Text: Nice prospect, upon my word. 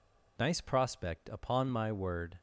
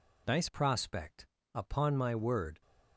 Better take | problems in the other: first | changes voice at "prospect"; from 0.4 s on; 2.2 s long

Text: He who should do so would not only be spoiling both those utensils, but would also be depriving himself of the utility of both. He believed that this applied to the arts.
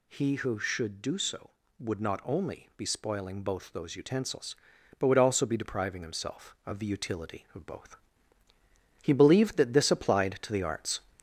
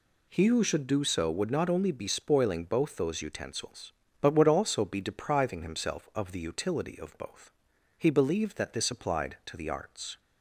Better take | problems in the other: second | gets louder; slight; throughout; 3 dB

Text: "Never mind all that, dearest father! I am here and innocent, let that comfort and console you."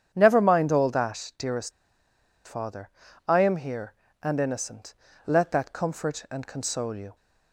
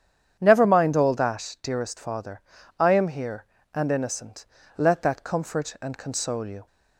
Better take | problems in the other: second | starts louder than the rest; strong; until 1.1 s; 9 dB; strong in the second // pauses between "dearest" and "father"; noticeable; at 1.7 s; 0.75 s long

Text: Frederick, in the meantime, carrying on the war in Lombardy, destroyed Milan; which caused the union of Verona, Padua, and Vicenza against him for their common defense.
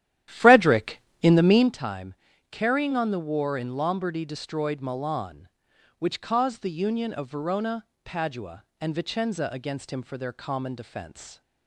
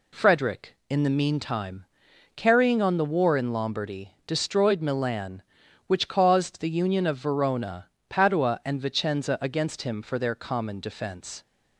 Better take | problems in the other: second | starts louder than the rest; strong; until 1.8 s; 11.5 dB

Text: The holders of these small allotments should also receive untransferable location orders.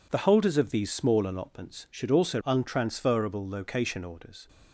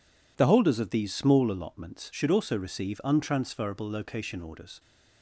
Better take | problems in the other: second | skips "receive"; at 2.4 s

